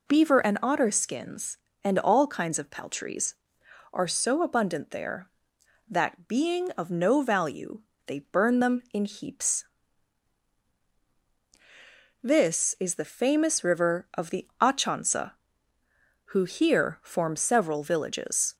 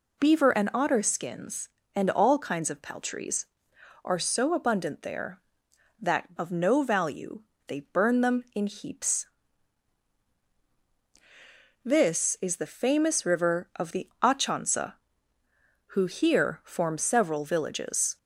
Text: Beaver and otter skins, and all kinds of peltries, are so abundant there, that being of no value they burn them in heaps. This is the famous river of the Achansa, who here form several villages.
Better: first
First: pauses between "value" and "they"; slight; at 7.8 s; 0.26 s long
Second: skips "being"; at 6.3 s // pauses between "value" and "they"; slight; at 7.4 s; 0.26 s long

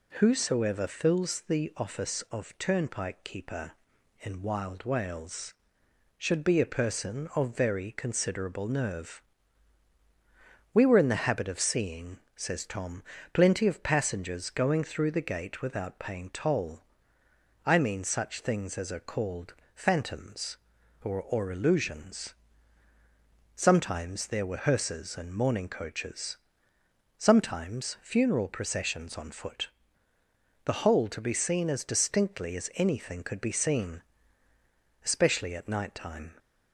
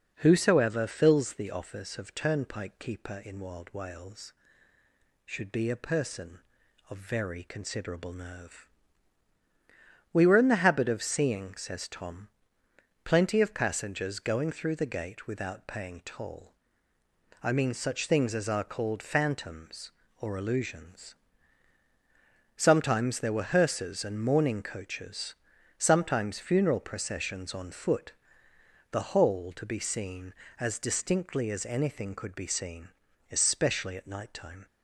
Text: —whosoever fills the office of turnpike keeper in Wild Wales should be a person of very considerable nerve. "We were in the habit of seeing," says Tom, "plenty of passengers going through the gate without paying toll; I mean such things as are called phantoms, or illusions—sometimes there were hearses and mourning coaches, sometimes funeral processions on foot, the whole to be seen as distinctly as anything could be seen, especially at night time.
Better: second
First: pauses between "called" and "phantoms"; slight; at 19.5 s; 0.20 s long // says "or" twice; at 21.2 s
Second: none

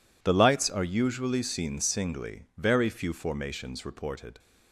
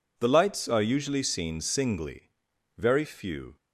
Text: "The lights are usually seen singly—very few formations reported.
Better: first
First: none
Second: stops before "formations reported"; at 3.5 s

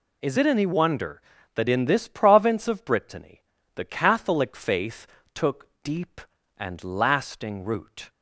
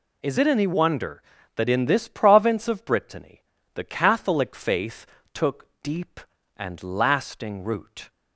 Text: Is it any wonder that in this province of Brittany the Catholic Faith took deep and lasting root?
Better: neither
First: pauses between "Brittany" and "the"; slight; at 3.4 s; 0.32 s long // pauses between "Faith" and "took"; slight; at 5.0 s; 0.28 s long // pauses between "took" and "deep"; slight; at 5.6 s; 0.16 s long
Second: pauses between "Brittany" and "the"; slight; at 3.4 s; 0.31 s long // pauses between "Faith" and "took"; slight; at 5.0 s; 0.28 s long // pauses between "took" and "deep"; slight; at 5.6 s; 0.16 s long

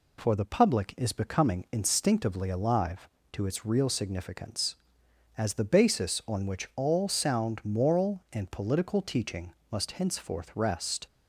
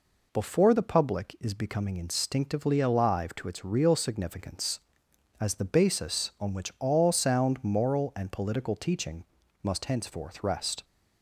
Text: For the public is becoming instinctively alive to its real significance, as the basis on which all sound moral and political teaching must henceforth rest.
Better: first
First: pauses between "teaching" and "must"; slight; at 9.5 s; 0.18 s long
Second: says "Before" for "For"; at 0.3 s // pauses between "teaching" and "must"; at 9.2 s; 0.40 s long

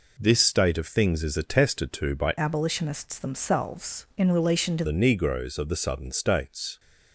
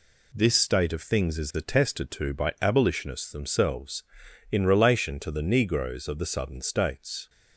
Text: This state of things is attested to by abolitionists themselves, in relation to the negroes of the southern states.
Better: second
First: changes voice from "abolitionists" to "to"; from 2.3 to 4.8 s; 2.5 s long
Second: none

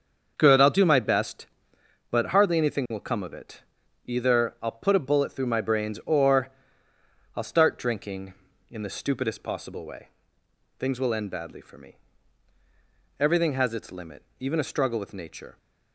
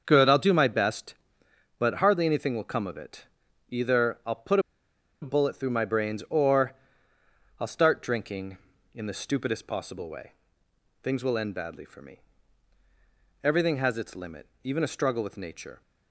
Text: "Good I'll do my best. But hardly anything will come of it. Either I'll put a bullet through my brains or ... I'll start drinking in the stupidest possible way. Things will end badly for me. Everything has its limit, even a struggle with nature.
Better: first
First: starts louder than the rest; until 1.3 s; 7 dB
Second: starts louder than the rest; until 1.0 s; 7 dB // pauses between "put" and "a"; noticeable; at 4.5 s; 0.62 s long

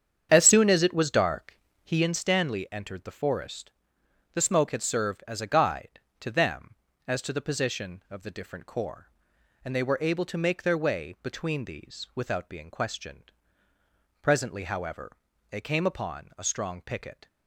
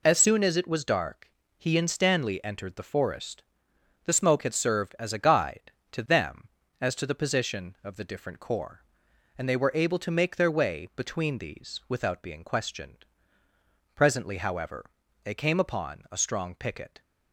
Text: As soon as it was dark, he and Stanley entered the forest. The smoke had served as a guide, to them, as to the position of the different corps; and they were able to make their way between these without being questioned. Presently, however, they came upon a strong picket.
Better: second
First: starts louder than the rest; strong; until 2.1 s; 8 dB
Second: none

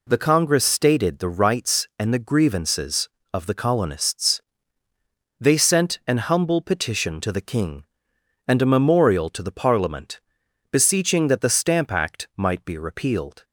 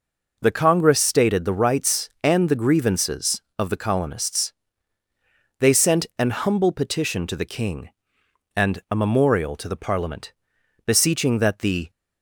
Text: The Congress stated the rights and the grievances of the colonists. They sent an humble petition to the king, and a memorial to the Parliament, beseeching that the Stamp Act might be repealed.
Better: first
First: none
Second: stops before "Stamp Act might be repealed"; at 11.8 s

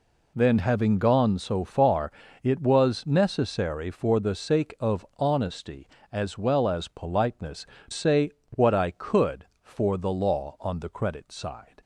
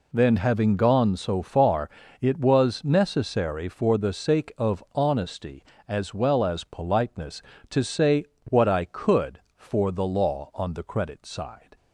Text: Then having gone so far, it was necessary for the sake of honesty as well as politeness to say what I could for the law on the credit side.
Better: second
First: skips "to"; at 7.7 s // pauses between "say" and "what"; slight; at 8.3 s; 0.20 s long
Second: pauses between "say" and "what"; slight; at 8.2 s; 0.20 s long

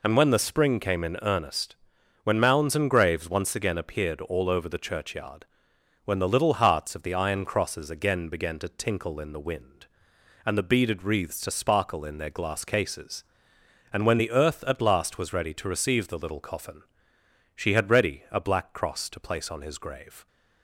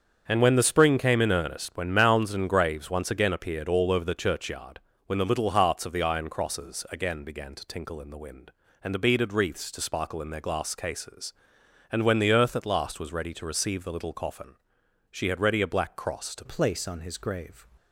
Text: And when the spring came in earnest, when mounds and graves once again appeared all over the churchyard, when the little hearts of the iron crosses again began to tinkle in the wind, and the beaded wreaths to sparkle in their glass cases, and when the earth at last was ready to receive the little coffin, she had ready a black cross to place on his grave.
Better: first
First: none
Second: starts louder than the rest; strong; until 1.2 s; 7 dB // changes voice at "place"; from 16.4 s on; 1.2 s long

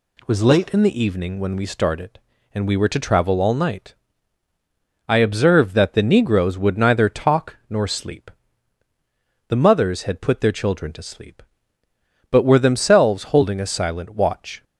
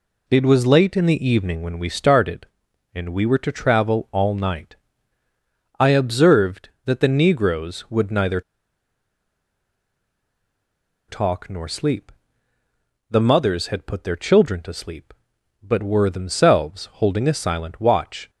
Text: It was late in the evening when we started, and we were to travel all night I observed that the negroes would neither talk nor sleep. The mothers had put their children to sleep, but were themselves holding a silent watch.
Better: first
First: pauses between "night" and "I"; at 3.9 s; 1.1 s long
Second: pauses between "night" and "I"; at 4.7 s; 1.0 s long // pauses between "neither" and "talk"; strong; at 8.4 s; 2.6 s long

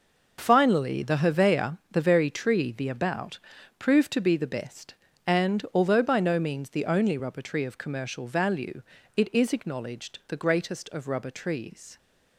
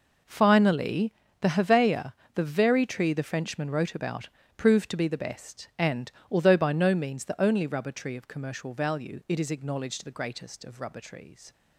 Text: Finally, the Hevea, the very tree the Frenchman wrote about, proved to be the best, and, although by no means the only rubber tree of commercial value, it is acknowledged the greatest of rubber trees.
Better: second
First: skips "Frenchman wrote"; at 2.8 s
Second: none

